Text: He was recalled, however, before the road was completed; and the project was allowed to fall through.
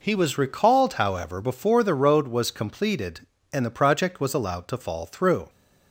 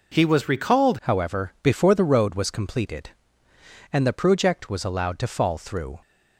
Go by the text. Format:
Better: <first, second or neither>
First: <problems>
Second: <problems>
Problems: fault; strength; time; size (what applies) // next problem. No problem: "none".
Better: first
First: none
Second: changes voice at "however"; from 1.0 s on; 4.9 s long